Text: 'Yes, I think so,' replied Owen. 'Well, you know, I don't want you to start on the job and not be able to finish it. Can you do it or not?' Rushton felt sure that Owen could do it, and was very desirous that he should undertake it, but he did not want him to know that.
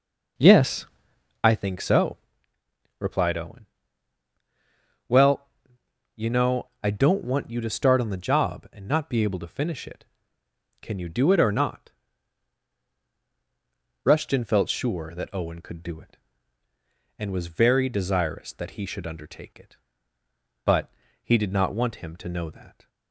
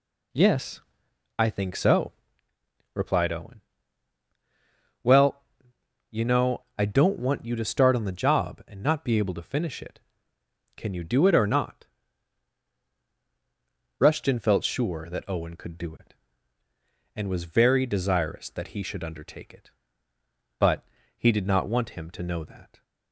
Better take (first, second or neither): second